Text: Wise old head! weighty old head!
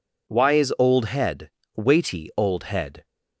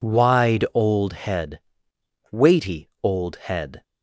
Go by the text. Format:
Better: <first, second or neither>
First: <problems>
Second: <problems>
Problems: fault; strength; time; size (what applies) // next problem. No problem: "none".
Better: first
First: none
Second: says "Wide" for "Wise"; at 0.0 s // pauses between "weighty" and "old"; slight; at 2.8 s; 0.16 s long